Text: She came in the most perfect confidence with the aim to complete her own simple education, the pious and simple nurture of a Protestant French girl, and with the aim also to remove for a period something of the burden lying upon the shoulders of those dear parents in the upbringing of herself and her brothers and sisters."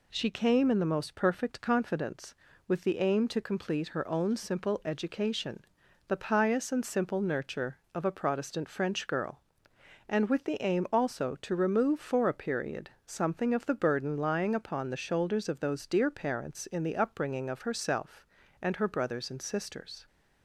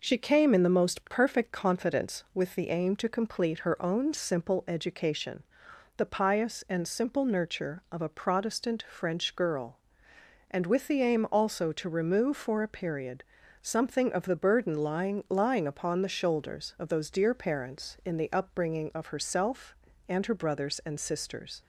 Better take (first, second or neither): first